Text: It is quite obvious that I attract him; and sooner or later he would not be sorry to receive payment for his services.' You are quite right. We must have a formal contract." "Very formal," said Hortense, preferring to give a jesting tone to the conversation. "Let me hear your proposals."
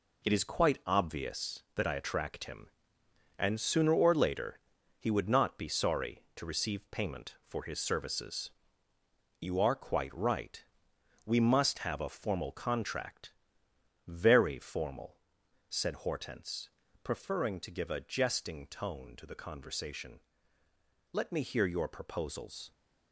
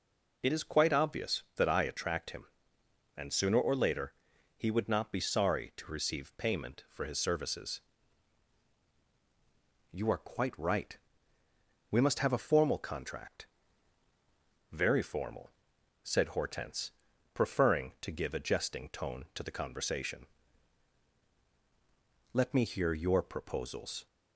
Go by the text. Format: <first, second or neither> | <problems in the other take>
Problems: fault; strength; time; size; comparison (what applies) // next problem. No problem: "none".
second | gets quieter; strong; throughout; 7.5 dB // pauses between "later" and "he"; at 4.5 s; 0.42 s long; also in the second